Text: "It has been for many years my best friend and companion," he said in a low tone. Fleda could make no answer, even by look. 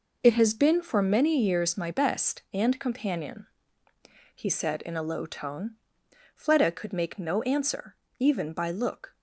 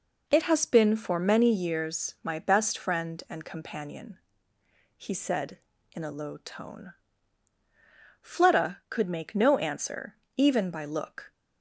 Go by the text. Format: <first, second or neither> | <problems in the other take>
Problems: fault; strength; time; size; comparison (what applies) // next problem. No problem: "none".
second | skips "friend"; at 2.4 s